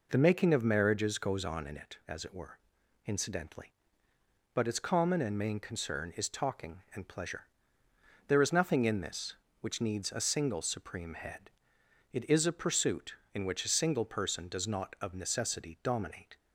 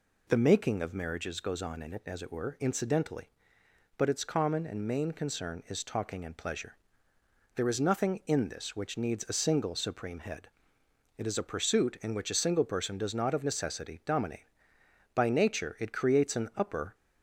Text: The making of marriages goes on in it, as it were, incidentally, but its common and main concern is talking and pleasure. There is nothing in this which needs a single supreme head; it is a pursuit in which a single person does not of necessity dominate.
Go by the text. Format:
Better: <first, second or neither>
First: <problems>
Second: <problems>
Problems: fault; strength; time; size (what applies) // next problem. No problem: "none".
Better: first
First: none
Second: goes on to say "By nature it creates an upper"; strong; from 15.1 s on; 1.8 s long